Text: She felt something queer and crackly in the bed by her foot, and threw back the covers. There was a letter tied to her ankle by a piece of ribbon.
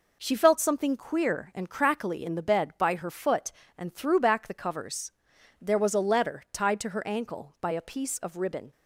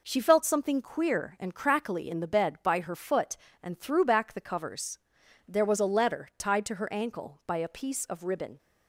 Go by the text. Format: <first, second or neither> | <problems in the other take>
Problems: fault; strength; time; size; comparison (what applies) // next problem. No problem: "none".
neither | none